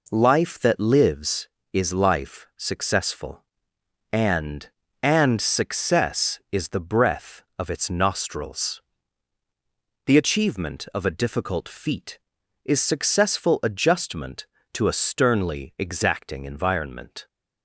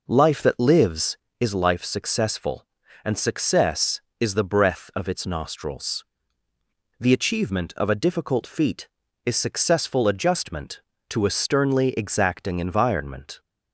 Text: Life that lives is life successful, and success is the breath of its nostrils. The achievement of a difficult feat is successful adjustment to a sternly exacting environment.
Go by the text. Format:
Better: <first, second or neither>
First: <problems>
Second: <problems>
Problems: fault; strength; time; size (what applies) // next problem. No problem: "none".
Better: second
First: says "and" twice; at 5.0 s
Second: none